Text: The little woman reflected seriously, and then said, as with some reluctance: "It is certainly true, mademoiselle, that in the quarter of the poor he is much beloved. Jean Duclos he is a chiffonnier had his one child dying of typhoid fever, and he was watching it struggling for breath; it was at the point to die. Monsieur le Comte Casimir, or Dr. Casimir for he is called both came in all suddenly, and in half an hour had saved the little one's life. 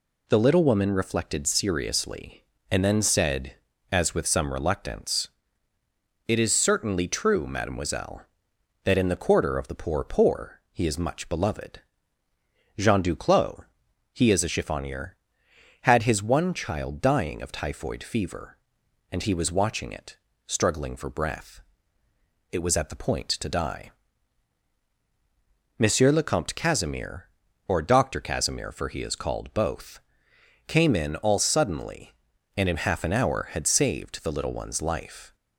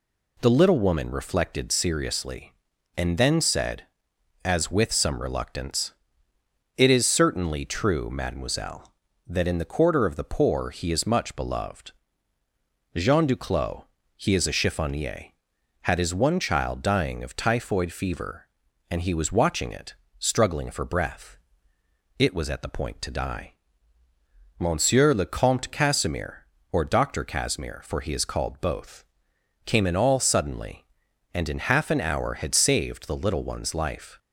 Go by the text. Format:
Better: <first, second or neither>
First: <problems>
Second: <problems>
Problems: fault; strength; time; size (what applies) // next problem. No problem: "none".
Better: second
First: says "poor" twice; at 10.0 s // pauses between "Duclos" and "he"; noticeable; at 13.6 s; 0.48 s long // pauses between "it" and "struggling"; slight; at 20.1 s; 0.30 s long // pauses between "both" and "came"; noticeable; at 30.0 s; 0.66 s long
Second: pauses between "Duclos" and "he"; slight; at 13.8 s; 0.32 s long // pauses between "it" and "struggling"; slight; at 19.9 s; 0.24 s long // pauses between "both" and "came"; noticeable; at 29.0 s; 0.62 s long